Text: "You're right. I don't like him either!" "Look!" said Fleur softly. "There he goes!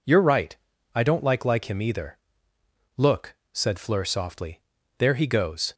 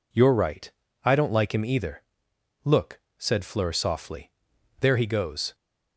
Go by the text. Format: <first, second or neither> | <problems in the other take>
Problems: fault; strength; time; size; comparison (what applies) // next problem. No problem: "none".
second | says "like" twice; at 1.4 s